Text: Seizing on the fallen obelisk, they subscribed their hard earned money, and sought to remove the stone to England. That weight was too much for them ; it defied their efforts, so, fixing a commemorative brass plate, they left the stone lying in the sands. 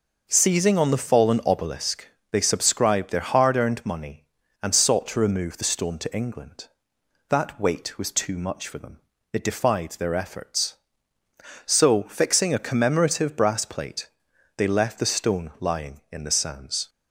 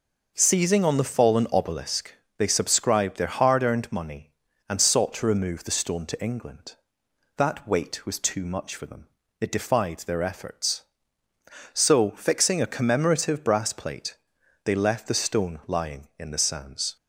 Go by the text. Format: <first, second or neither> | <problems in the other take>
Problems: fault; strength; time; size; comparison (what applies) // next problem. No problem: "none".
neither | none